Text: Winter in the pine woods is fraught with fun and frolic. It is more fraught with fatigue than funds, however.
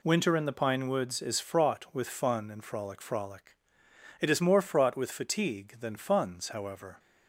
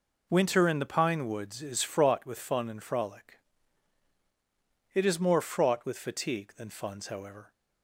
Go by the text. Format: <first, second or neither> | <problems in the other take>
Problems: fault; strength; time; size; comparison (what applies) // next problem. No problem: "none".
second | says "frolic" twice; at 3.0 s